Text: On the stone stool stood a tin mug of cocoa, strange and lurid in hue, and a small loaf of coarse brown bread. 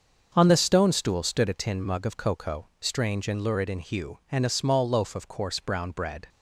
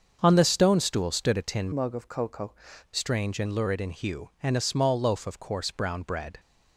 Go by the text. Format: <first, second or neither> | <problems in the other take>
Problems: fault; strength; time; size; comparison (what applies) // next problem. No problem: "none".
first | starts louder than the rest; until 1.2 s; 6.5 dB; also in the first // changes voice from "mug" to "cocoa"; from 1.7 to 2.5 s; 0.8 s long